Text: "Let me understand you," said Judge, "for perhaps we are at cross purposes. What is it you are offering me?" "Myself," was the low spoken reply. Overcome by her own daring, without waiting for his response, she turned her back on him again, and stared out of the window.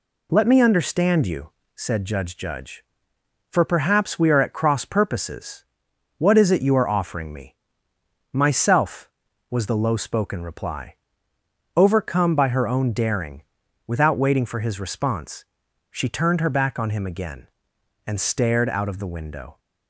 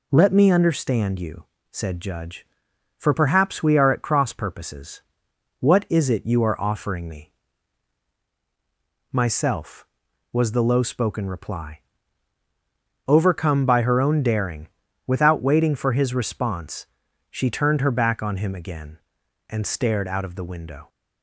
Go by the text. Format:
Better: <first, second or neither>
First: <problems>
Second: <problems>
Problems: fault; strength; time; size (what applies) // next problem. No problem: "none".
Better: second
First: says "Judge" twice; at 2.3 s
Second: none